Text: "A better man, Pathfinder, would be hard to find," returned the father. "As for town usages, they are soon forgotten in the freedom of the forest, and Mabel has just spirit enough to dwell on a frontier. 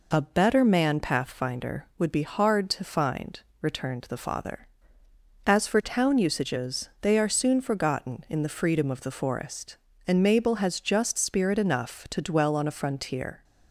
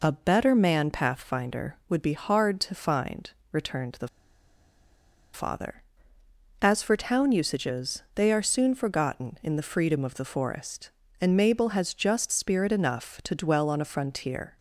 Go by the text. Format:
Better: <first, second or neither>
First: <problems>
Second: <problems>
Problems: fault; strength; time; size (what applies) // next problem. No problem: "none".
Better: first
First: none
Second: pauses between "the" and "father"; strong; at 4.0 s; 1.2 s long